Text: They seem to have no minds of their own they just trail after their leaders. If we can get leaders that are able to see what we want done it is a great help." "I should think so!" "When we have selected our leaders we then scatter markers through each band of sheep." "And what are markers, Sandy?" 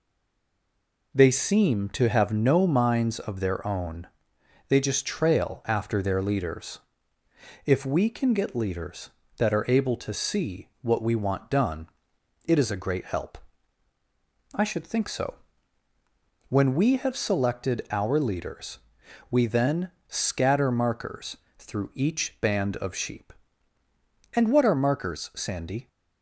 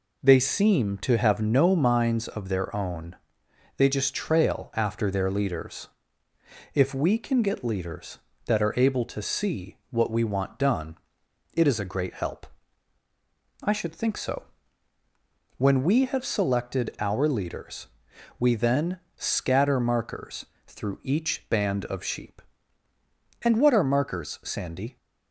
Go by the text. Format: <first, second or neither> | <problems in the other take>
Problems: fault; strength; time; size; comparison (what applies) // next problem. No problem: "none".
second | stays silent before the first word; until 1.1 s; 1.1 s long // pauses between "own" and "they"; noticeable; at 4.0 s; 0.62 s long; noticeable in the second // pauses between "done" and "it"; noticeable; at 11.8 s; 0.56 s long; noticeable in the second // pauses between "leaders" and "we"; noticeable; at 18.7 s; 0.52 s long; noticeable in the second // pauses between "then" and "scatter"; slight; at 19.9 s; 0.16 s long; slight in the second // pauses between "markers" and "through"; slight; at 21.3 s; 0.20 s long; slight in the second